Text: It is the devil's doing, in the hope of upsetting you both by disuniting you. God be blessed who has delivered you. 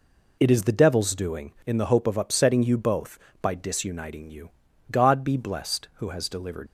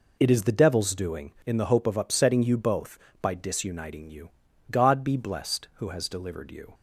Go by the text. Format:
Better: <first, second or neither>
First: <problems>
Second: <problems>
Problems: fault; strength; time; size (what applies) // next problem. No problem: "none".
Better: second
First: stops before "you"; at 6.6 s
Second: none